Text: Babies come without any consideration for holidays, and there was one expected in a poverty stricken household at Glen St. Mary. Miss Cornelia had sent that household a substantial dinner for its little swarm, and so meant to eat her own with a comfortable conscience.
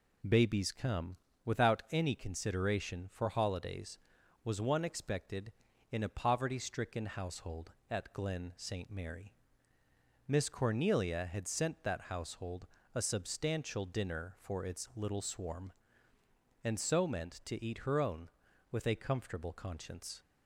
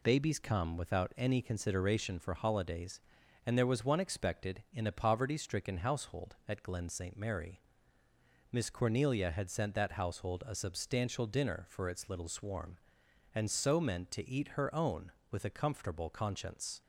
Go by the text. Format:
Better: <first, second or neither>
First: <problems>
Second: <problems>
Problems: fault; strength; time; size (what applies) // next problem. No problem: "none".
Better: second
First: pauses between "come" and "without"; slight; at 1.1 s; 0.30 s long // skips "and there"; at 4.2 s // pauses between "household" and "a"; slight; at 12.6 s; 0.26 s long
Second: none